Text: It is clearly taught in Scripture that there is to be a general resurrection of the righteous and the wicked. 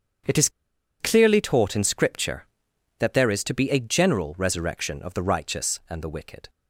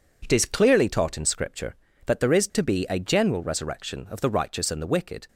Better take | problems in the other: second | starts louder than the rest; strong; until 1.7 s; 7.5 dB // pauses between "is" and "clearly"; noticeable; at 0.4 s; 0.51 s long

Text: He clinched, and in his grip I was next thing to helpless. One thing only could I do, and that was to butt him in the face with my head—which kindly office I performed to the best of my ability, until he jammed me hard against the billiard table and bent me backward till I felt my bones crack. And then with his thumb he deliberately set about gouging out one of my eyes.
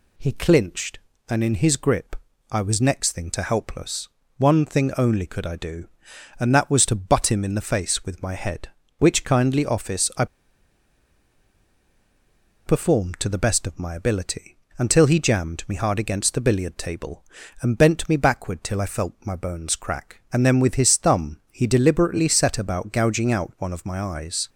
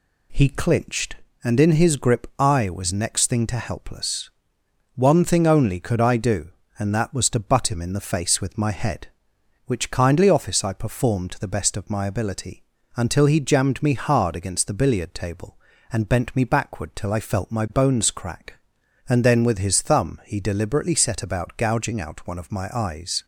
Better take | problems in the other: second | pauses between "grip" and "I"; slight; at 2.1 s; 0.36 s long // pauses between "I" and "performed"; strong; at 10.2 s; 2.4 s long

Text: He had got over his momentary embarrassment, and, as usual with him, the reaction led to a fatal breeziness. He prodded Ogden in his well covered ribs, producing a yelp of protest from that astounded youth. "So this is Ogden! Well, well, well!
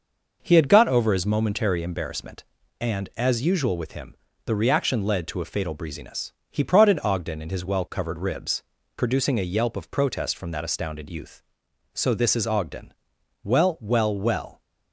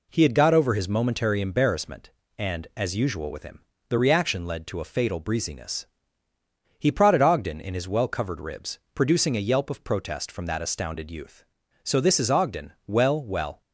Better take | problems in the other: first | stops before "well"; at 13.6 s

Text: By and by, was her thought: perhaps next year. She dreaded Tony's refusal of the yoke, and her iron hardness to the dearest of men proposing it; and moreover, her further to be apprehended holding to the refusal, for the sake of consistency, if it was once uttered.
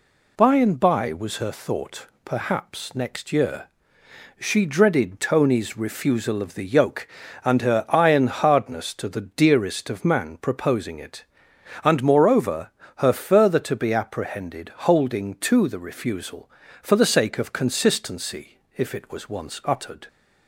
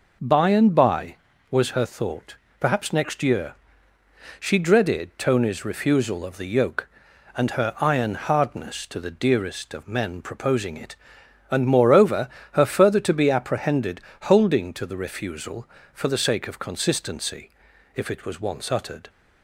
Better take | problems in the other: second | says "man" for "men"; at 10.0 s // pauses between "apprehended" and "holding"; slight; at 14.7 s; 0.16 s long; slight in the second

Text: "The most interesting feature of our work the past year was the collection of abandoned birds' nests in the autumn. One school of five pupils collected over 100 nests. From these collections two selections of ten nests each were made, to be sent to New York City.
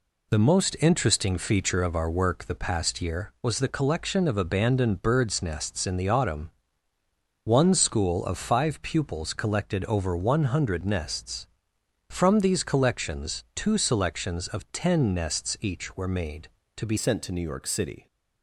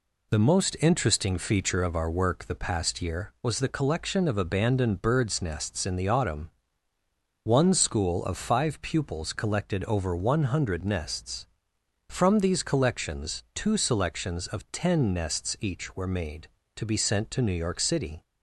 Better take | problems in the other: second | changes voice at "sent"; from 16.9 s on; 1.1 s long

